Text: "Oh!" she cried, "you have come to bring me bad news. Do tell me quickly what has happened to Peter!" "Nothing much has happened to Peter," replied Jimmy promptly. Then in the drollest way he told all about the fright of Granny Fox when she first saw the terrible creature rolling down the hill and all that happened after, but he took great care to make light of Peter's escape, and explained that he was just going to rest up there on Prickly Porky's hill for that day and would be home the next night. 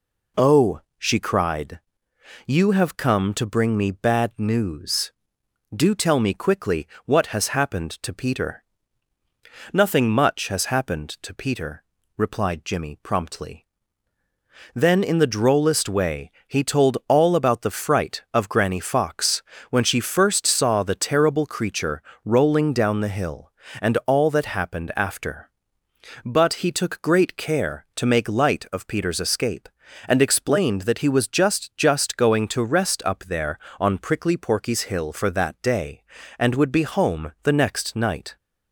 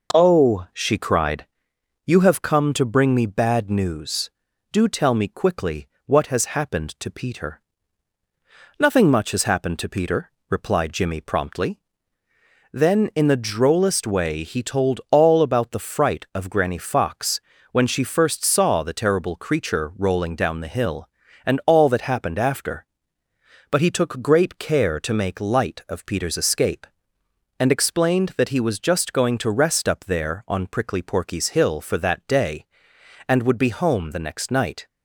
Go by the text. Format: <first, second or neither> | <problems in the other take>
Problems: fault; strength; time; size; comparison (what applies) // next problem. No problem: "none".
second | pauses between "quickly" and "what"; slight; at 6.8 s; 0.18 s long; slight in the second // pauses between "way" and "he"; slight; at 16.3 s; 0.18 s long // pauses between "Fox" and "when"; slight; at 19.4 s; 0.28 s long; slight in the second // pauses between "creature" and "rolling"; slight; at 22.0 s; 0.22 s long // says "just" twice; at 31.7 s